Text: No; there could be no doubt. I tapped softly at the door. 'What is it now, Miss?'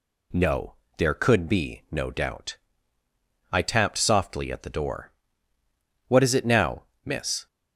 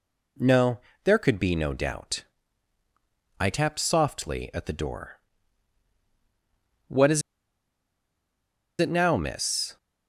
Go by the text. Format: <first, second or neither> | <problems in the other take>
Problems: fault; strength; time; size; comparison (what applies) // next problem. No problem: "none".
first | pauses between "is" and "it"; strong; at 7.2 s; 1.5 s long